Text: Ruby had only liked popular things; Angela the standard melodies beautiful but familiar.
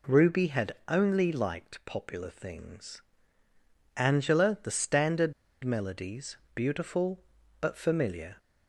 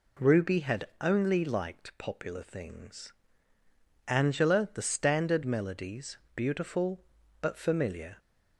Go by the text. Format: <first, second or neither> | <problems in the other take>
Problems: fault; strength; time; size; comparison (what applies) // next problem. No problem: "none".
second | pauses between "standard" and "melodies"; slight; at 5.3 s; 0.30 s long // pauses between "melodies" and "beautiful"; slight; at 6.3 s; 0.18 s long; slight in the second